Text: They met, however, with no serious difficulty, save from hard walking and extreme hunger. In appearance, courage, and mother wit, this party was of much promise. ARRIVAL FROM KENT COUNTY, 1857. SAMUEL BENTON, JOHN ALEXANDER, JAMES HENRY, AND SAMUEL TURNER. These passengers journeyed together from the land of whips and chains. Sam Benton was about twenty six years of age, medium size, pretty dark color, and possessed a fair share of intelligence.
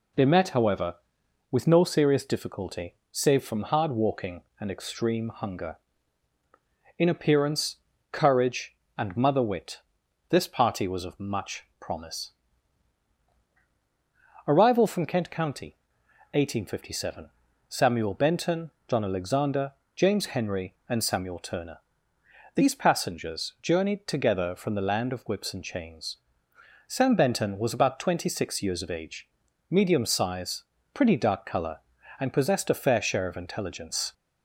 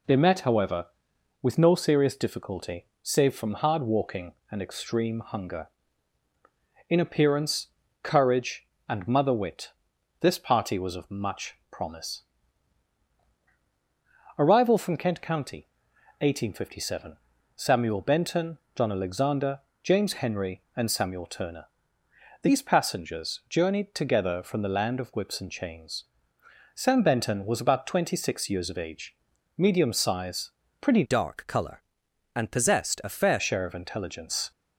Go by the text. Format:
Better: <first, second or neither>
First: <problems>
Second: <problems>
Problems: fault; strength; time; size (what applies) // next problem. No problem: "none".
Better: first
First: pauses between "much" and "promise"; slight; at 11.6 s; 0.16 s long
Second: pauses between "much" and "promise"; slight; at 11.5 s; 0.16 s long // changes voice from "dark" to "fair"; from 31.0 to 33.3 s; 2.3 s long